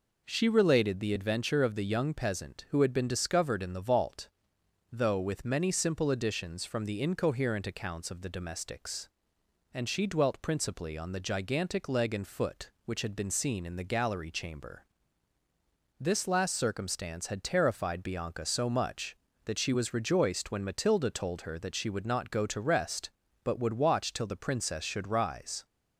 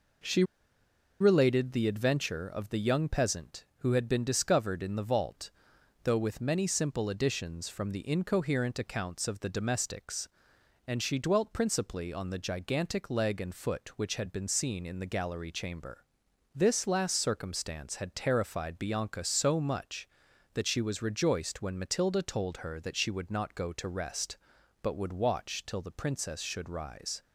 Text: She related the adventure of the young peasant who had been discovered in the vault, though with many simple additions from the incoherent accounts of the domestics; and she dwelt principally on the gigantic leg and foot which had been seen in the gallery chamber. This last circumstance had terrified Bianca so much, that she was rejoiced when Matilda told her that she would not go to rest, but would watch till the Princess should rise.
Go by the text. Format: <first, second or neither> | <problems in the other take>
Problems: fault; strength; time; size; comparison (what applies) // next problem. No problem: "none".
first | pauses between "She" and "related"; noticeable; at 0.4 s; 0.76 s long